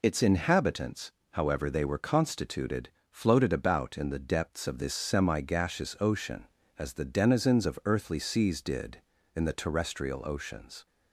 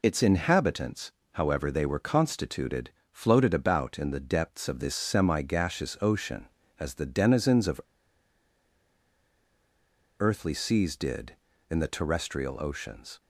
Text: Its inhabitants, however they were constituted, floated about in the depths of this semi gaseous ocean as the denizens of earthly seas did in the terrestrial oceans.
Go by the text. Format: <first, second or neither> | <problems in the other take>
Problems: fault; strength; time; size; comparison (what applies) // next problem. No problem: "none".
first | pauses between "of" and "earthly"; strong; at 7.8 s; 2.3 s long